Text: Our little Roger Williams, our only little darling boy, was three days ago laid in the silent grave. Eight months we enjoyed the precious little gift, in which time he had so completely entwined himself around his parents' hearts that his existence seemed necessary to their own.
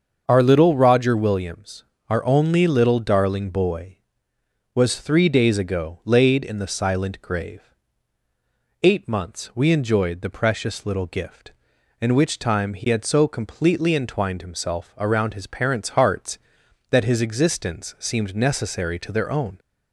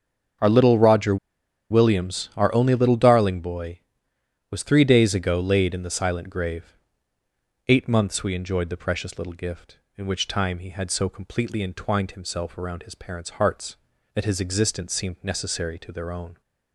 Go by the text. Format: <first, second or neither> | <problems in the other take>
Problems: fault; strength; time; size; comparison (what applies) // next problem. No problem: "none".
first | starts louder than the rest; until 1.9 s; 7 dB; also in the first // pauses between "Roger" and "Williams"; noticeable; at 1.1 s; 0.53 s long